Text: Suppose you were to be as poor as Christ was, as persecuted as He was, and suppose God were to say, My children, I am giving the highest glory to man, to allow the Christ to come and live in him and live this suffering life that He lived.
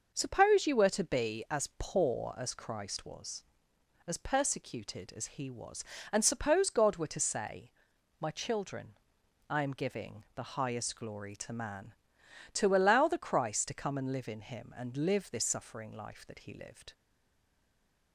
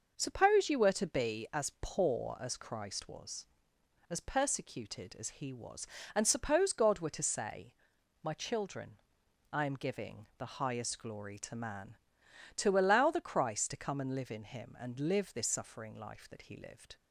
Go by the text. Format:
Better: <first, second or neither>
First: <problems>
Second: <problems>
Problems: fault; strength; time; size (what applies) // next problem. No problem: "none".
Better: second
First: stays silent after the last word; noticeable; from 16.9 s on; 1.2 s long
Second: none